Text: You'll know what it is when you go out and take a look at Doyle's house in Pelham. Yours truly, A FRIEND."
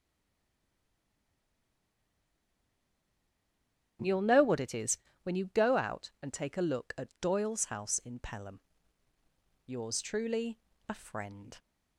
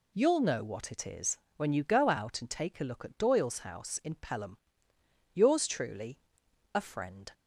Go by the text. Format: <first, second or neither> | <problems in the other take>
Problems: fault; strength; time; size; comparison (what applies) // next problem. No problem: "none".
second | stays silent before the first word; strong; until 3.9 s; 3.9 s long // starts louder than the rest; strong; until 5.3 s; 9.5 dB // pauses between "is" and "when"; slight; at 4.9 s; 0.28 s long; slight in the second